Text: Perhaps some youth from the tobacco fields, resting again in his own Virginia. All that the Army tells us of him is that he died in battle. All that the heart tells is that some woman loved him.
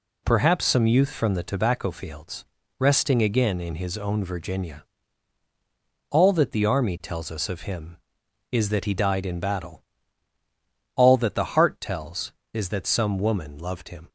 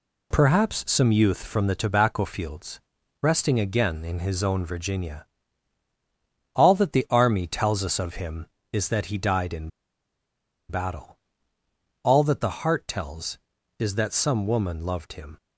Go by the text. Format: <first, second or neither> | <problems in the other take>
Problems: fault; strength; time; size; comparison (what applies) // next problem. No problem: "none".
first | pauses between "in" and "battle"; at 9.6 s; 1.0 s long